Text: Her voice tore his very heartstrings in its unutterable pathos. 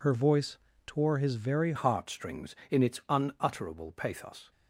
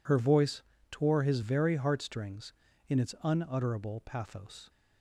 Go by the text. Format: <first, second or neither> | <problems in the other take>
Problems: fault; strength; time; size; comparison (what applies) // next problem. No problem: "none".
second | pauses between "voice" and "tore"; slight; at 0.5 s; 0.30 s long; slight in the second // changes voice at "heartstrings"; from 1.7 s on; 2.8 s long